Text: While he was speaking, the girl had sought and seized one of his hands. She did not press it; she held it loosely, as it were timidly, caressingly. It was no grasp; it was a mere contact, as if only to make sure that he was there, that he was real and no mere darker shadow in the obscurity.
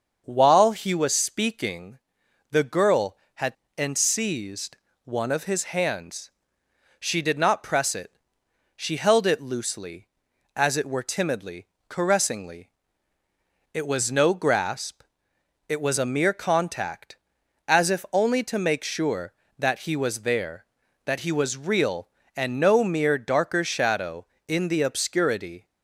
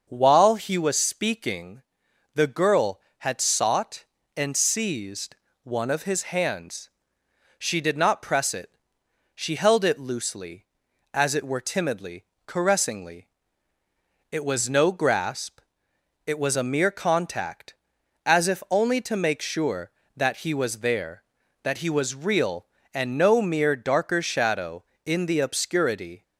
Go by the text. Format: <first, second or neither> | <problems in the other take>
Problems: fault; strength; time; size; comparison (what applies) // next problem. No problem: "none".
second | starts louder than the rest; until 1.2 s; 6.5 dB; also in the second // skips "sought"; at 3.6 s // pauses between "seized" and "one"; slight; at 4.7 s; 0.30 s long; slight in the second